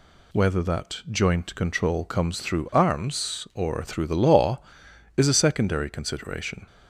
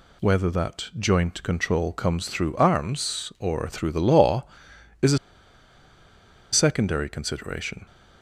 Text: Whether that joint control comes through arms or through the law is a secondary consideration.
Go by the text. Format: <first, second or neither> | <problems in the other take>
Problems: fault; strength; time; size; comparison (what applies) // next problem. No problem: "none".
first | pauses between "a" and "secondary"; strong; at 5.1 s; 1.3 s long